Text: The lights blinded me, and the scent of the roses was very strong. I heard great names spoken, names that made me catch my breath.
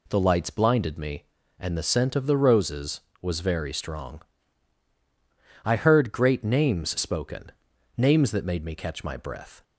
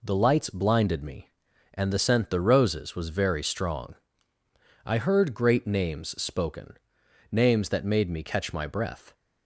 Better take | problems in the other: first | skips "of"; at 2.3 s

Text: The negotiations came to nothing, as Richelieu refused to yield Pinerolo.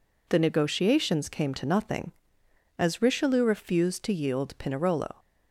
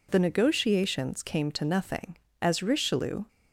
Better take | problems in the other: first | stops before "refused to yield Pinerolo"; at 3.2 s

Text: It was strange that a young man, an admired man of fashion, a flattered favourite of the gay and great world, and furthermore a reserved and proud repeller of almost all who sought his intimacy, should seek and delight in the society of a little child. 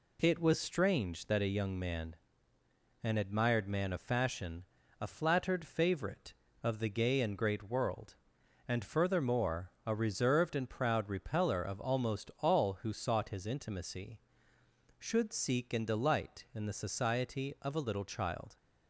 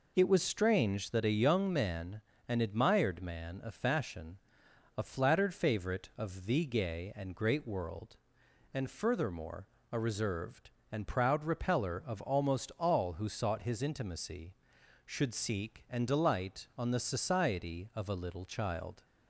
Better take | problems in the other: first | pauses between "furthermore" and "a"; slight; at 9.6 s; 0.26 s long; slight in the first // says "on" for "in"; at 16.7 s

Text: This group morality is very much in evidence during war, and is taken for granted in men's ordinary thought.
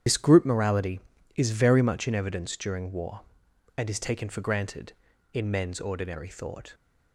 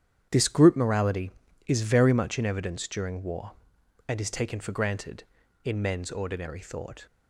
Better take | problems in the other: second | loses the start of "This"; at 0.0 s; 70 ms // starts louder than the rest; strong; until 1.4 s; 9 dB; strong in the second

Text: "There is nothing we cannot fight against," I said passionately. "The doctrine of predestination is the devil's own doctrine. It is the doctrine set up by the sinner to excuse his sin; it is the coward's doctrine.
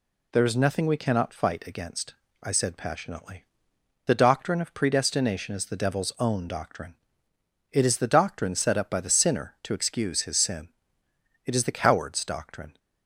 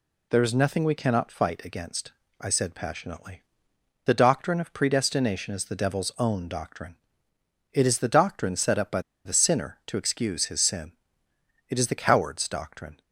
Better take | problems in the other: first | pauses between "by" and "the"; slight; at 9.0 s; 0.24 s long

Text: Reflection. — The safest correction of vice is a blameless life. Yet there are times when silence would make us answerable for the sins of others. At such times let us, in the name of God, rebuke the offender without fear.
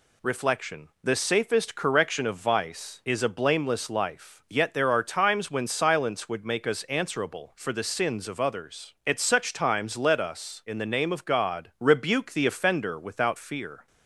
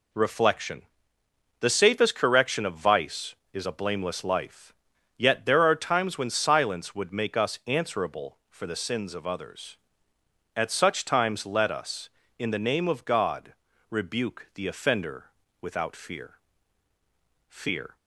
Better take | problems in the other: first | pauses between "offender" and "without"; slight; at 15.2 s; 0.36 s long // says "fear" twice; at 17.4 s

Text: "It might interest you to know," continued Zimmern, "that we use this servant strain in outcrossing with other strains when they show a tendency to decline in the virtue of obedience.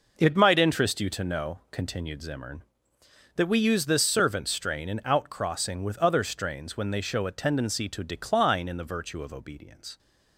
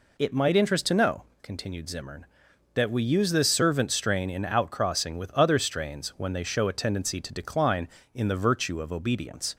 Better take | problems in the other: first | skips "you"; at 0.8 s

